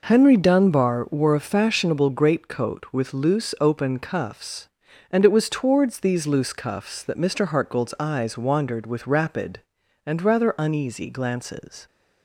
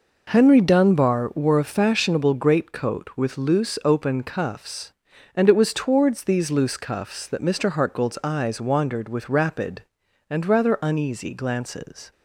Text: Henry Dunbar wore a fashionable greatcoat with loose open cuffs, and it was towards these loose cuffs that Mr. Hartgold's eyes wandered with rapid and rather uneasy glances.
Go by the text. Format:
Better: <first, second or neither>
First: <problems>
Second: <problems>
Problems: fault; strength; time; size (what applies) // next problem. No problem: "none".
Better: neither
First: none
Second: none